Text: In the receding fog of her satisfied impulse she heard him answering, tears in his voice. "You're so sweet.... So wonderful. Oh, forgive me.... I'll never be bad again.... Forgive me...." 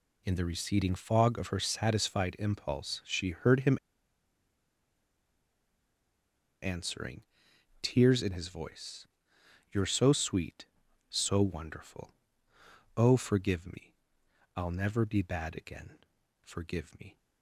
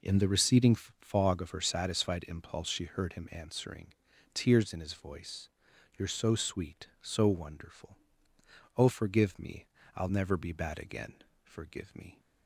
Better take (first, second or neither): second